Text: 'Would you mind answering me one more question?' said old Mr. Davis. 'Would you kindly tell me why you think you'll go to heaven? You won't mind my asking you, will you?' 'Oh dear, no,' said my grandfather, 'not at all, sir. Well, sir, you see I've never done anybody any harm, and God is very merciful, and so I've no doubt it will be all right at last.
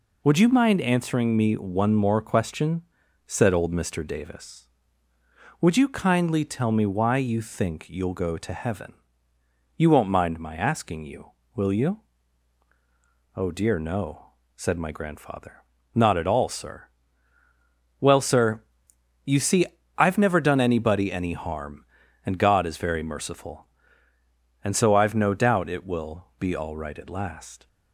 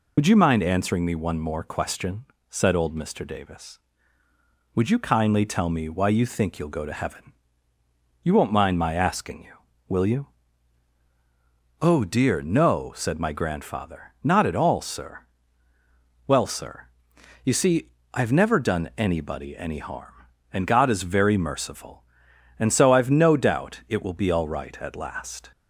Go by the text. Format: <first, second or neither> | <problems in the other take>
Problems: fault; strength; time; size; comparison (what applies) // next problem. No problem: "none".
first | loses the start of "Would"; at 0.1 s; 40 ms // pauses between "see" and "I've"; slight; at 17.8 s; 0.26 s long; slight in the first